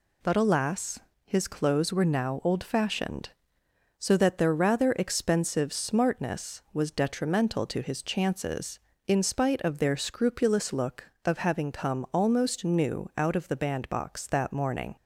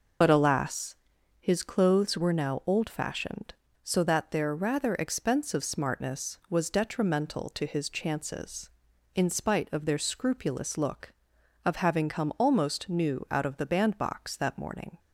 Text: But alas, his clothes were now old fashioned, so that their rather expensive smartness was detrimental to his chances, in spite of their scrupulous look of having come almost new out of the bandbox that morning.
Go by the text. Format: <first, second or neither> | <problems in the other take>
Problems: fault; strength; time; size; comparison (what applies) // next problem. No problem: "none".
first | loses the start of "But"; at 0.2 s; 50 ms